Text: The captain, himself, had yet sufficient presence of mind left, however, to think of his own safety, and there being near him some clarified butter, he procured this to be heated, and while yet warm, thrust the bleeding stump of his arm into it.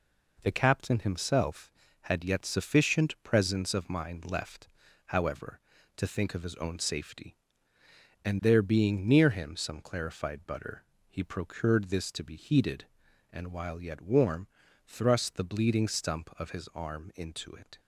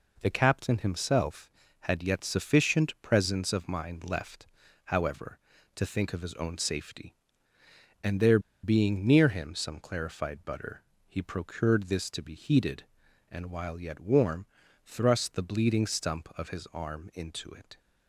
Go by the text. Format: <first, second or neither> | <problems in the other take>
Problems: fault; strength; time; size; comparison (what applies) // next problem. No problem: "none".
first | pauses between "there" and "being"; slight; at 8.3 s; 0.24 s long